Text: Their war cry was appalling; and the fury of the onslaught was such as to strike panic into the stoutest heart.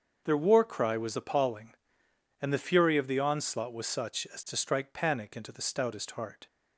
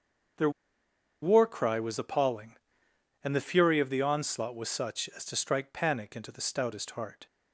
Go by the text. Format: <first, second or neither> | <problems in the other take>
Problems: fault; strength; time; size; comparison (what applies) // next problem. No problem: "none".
first | starts louder than the rest; until 2.1 s; 6.5 dB; also in the first // pauses between "Their" and "war"; noticeable; at 0.4 s; 0.72 s long